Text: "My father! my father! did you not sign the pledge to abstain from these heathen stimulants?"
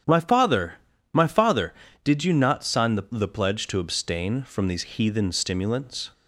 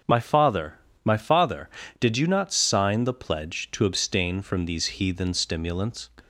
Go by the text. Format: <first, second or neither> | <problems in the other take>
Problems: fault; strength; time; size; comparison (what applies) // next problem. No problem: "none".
second | starts louder than the rest; strong; until 1.4 s; 9 dB; also in the second // says "the" twice; at 3.0 s